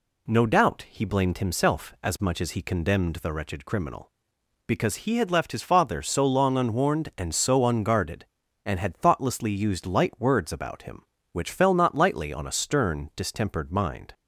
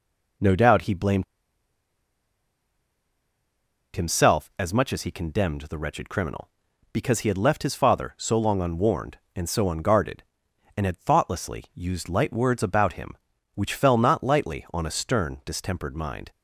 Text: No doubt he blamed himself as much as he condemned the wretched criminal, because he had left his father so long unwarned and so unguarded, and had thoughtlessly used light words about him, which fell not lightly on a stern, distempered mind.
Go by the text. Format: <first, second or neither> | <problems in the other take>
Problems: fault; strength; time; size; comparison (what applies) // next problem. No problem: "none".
first | pauses between "blamed" and "himself"; strong; at 1.2 s; 2.7 s long